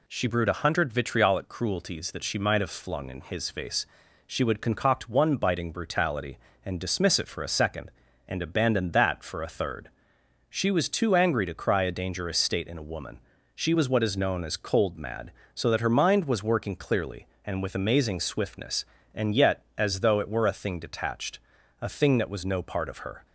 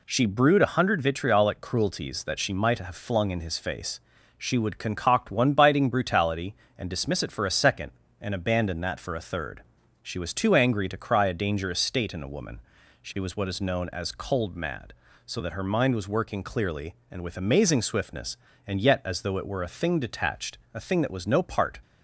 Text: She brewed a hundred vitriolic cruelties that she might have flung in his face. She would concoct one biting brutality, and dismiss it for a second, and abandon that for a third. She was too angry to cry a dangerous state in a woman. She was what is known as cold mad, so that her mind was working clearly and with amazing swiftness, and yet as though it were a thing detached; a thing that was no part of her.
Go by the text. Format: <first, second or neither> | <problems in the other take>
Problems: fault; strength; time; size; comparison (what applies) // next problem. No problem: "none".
first | stops before "of her"; at 21.8 s